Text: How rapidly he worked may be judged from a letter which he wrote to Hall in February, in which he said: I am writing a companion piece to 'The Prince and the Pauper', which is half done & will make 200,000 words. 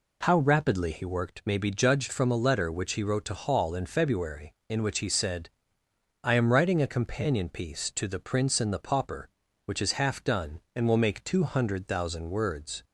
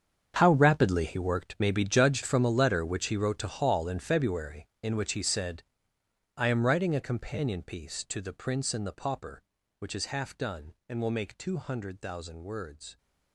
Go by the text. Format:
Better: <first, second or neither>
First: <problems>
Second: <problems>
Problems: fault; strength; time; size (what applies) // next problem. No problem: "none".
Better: first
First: none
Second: gets quieter; strong; throughout; 15.5 dB